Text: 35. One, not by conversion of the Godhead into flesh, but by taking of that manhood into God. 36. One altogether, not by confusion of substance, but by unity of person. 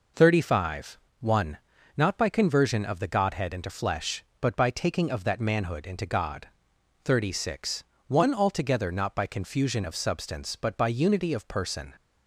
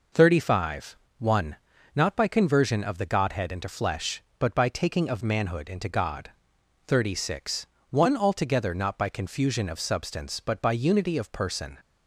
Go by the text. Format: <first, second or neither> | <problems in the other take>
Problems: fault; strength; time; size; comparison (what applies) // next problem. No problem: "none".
first | skips "that"; at 5.2 s